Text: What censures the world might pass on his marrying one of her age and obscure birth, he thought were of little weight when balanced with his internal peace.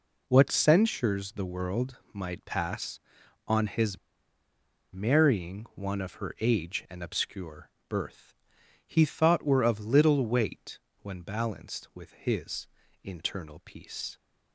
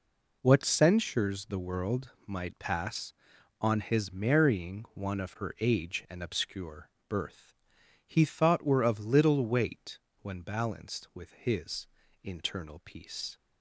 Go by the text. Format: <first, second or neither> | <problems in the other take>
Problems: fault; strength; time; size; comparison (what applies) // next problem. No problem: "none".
second | pauses between "his" and "marrying"; noticeable; at 3.9 s; 0.96 s long // pauses between "obscure" and "birth"; slight; at 7.6 s; 0.22 s long; slight in the second // pauses between "weight" and "when"; slight; at 10.7 s; 0.24 s long; slight in the second // pauses between "his" and "internal"; slight; at 12.6 s; 0.34 s long; slight in the second